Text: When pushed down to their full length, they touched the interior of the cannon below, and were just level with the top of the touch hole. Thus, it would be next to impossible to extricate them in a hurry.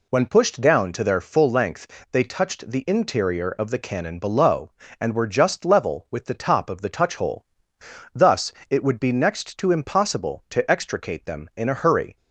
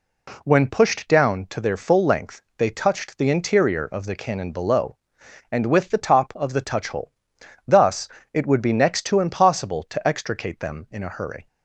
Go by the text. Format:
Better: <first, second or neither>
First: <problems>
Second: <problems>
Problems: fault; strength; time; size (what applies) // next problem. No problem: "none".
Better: first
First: none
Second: skips "were just level"; at 5.6 s